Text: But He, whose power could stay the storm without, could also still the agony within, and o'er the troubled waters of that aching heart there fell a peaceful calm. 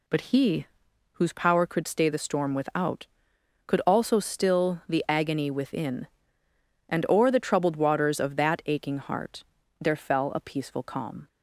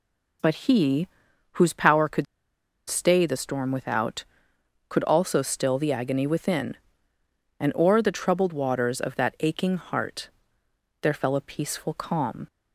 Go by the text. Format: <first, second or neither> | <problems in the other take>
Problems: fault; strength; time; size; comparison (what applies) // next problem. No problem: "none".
first | pauses between "could" and "stay"; noticeable; at 2.2 s; 0.63 s long // pauses between "heart" and "there"; noticeable; at 10.2 s; 0.72 s long; also in the first